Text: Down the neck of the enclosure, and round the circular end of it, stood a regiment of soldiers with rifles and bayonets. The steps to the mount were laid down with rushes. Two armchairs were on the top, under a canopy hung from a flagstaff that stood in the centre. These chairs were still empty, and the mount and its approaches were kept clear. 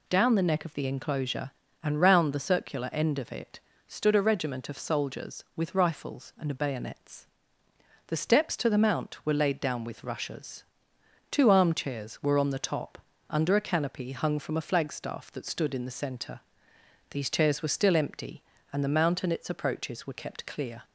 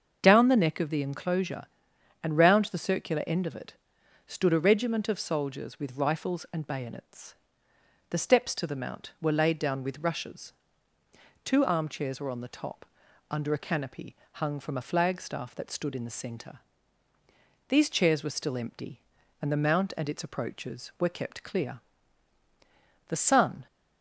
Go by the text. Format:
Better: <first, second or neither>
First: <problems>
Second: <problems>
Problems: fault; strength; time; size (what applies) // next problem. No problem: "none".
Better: first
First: none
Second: starts louder than the rest; until 1.2 s; 6.5 dB // pauses between "canopy" and "hung"; slight; at 14.1 s; 0.16 s long // goes on to say "The sun"; from 23.0 s on; 0.58 s long